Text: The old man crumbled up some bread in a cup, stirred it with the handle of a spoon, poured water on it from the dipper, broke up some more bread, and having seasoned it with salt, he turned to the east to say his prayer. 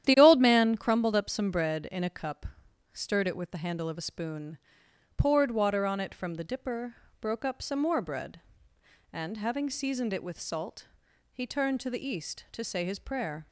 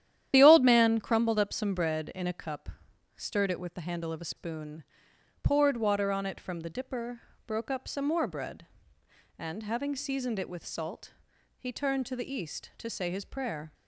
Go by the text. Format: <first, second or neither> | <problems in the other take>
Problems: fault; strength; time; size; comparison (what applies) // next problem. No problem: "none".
first | loses the start of "The"; at 0.3 s; 40 ms // starts louder than the rest; strong; until 1.3 s; 11 dB; strong in the first